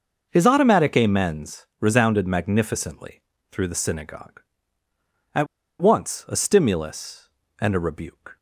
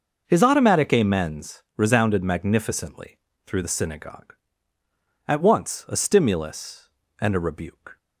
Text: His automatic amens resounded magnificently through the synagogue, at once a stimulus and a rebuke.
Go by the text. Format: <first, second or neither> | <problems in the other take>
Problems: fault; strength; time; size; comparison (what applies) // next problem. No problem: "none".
second | pauses between "amens" and "resounded"; slight; at 1.6 s; 0.16 s long; slight in the second // pauses between "magnificently" and "through"; slight; at 3.2 s; 0.28 s long; slight in the second // pauses between "at" and "once"; slight; at 5.4 s; 0.34 s long